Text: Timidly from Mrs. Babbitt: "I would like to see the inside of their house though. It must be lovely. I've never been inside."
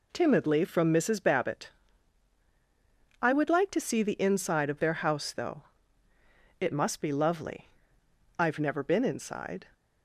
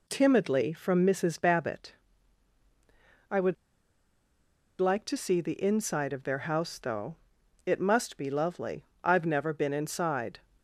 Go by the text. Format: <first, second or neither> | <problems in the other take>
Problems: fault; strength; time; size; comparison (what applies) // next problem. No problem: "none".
first | pauses between "would" and "like"; strong; at 3.5 s; 1.2 s long